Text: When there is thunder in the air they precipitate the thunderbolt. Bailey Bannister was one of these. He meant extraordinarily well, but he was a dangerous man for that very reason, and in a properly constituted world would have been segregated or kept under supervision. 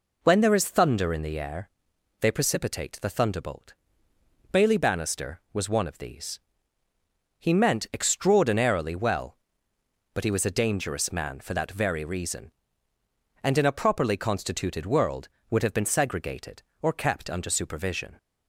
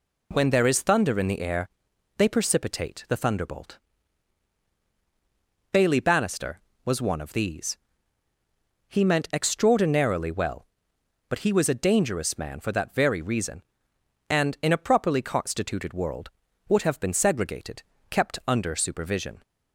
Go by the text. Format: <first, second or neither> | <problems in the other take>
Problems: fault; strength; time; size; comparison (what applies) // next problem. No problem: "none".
first | pauses between "air" and "they"; noticeable; at 1.6 s; 0.48 s long; noticeable in the first // skips "or"; at 17.9 s